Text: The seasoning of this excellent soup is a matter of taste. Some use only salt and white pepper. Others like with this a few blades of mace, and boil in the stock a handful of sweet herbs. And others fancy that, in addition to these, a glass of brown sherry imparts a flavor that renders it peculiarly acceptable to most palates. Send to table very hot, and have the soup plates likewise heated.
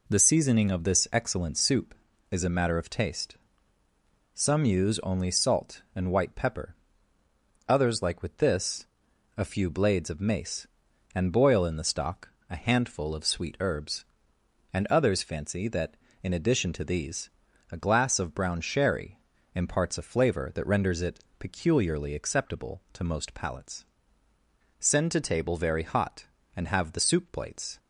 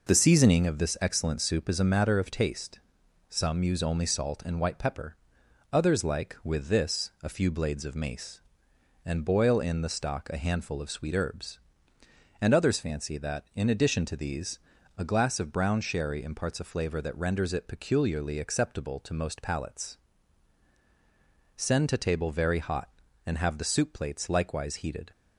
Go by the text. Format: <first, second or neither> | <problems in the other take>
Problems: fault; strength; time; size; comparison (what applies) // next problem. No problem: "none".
second | pauses between "this" and "a"; noticeable; at 8.8 s; 0.50 s long // pauses between "stock" and "a"; slight; at 12.2 s; 0.20 s long // pauses between "sherry" and "imparts"; slight; at 19.1 s; 0.36 s long // pauses between "it" and "peculiarly"; slight; at 21.1 s; 0.20 s long // stops before "likewise heated"; at 27.7 s